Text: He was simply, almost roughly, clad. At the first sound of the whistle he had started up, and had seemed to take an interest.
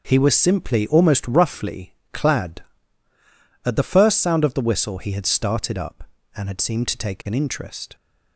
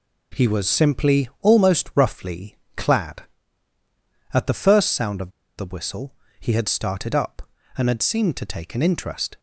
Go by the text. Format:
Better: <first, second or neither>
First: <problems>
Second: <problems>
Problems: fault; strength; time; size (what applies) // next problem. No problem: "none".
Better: first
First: none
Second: pauses between "of" and "the"; slight; at 5.2 s; 0.28 s long // pauses between "whistle" and "he"; slight; at 6.1 s; 0.26 s long